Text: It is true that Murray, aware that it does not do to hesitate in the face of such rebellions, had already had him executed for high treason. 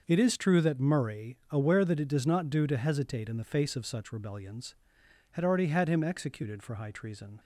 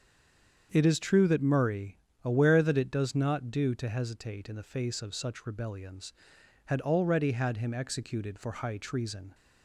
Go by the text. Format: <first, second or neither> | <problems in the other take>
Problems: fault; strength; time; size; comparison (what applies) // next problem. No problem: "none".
first | stays silent before the first word; slight; until 0.7 s; 0.7 s long // starts louder than the rest; strong; until 1.7 s; 7.5 dB; noticeable in the first